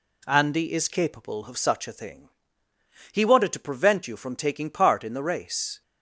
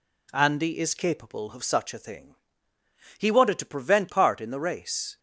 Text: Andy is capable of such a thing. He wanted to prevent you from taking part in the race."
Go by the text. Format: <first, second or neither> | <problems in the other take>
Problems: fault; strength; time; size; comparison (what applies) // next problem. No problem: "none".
first | skips "you from taking"; at 4.0 s